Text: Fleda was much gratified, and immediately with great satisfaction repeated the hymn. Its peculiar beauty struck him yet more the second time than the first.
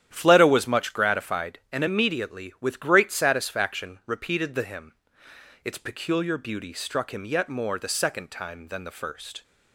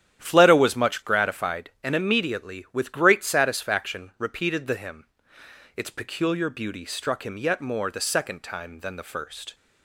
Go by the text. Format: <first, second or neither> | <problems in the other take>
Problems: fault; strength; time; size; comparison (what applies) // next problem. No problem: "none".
neither | starts louder than the rest; strong; the same in both